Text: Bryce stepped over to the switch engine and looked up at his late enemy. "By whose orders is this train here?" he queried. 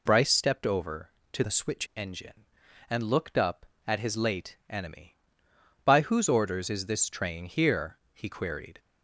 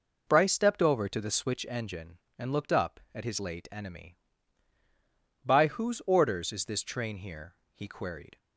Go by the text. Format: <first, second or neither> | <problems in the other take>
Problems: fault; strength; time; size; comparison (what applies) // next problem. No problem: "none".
second | changes voice from "the" to "switch"; from 1.4 to 1.8 s; 0.4 s long